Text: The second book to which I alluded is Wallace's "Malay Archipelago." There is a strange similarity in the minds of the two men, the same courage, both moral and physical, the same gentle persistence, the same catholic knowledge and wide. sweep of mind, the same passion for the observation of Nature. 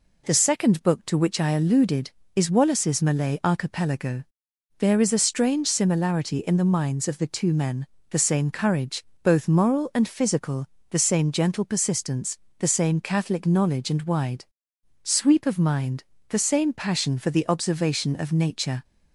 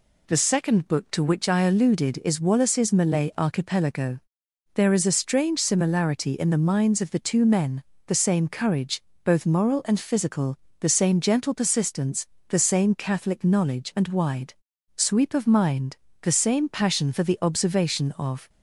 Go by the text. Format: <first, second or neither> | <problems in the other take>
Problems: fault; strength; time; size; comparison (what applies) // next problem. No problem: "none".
first | stops before "Nature"; at 18.4 s